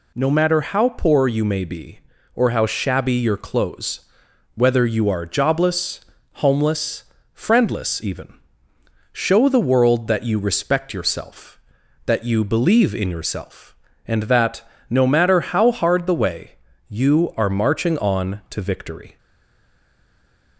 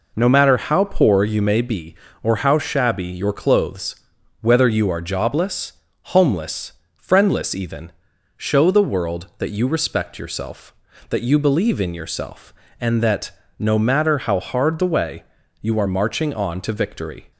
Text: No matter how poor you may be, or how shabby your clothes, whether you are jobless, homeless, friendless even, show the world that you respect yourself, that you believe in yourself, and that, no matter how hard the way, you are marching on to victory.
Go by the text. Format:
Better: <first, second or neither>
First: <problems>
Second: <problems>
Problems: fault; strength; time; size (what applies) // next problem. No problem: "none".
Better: second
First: stays silent after the last word; noticeable; from 19.1 s on; 1.4 s long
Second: none